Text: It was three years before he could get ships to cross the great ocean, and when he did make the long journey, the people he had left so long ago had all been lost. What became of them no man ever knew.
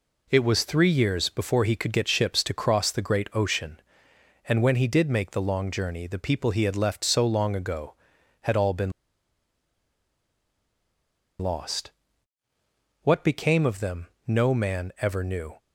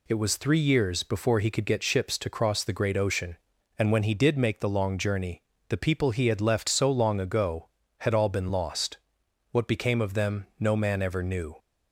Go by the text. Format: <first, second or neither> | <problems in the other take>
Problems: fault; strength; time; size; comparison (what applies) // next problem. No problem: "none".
second | pauses between "been" and "lost"; strong; at 8.9 s; 2.4 s long // pauses between "them" and "no"; slight; at 14.0 s; 0.20 s long